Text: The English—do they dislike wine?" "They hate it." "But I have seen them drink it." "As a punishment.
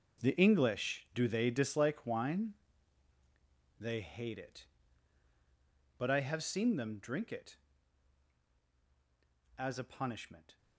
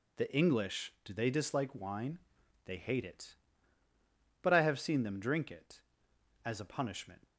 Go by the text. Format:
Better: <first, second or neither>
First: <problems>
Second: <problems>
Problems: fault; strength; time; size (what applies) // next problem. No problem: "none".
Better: second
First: gets quieter; strong; throughout; 13.5 dB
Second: none